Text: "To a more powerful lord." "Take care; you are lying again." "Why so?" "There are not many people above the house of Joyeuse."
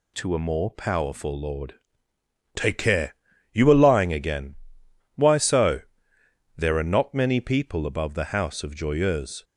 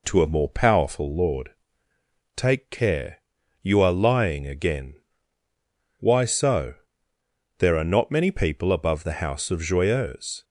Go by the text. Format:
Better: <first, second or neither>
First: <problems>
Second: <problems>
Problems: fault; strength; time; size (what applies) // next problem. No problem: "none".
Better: neither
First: none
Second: none